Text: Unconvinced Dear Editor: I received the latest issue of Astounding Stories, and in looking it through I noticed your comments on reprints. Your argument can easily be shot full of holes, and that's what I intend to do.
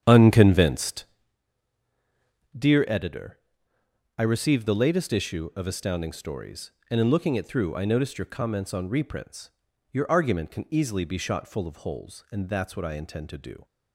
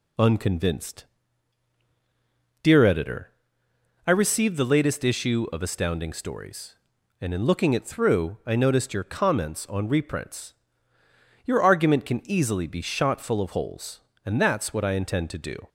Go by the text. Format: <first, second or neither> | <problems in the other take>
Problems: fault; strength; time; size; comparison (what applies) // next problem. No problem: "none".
second | starts louder than the rest; strong; until 1.4 s; 9 dB // pauses between "Unconvinced" and "Dear"; strong; at 1.0 s; 1.5 s long; strong in the second